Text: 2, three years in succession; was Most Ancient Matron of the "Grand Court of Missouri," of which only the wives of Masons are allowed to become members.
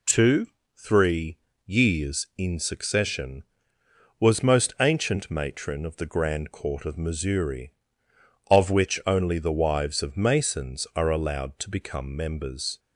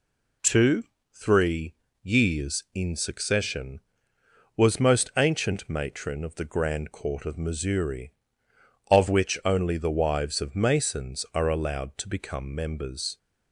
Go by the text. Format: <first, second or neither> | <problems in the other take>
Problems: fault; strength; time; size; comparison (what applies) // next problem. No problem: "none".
neither | pauses between "three" and "years"; slight; the same in both